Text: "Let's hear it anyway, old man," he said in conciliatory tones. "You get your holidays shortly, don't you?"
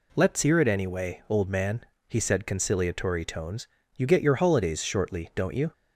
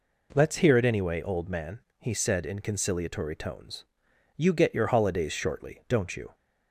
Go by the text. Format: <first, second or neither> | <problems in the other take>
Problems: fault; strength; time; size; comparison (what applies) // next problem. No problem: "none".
second | skips "in"; at 2.4 s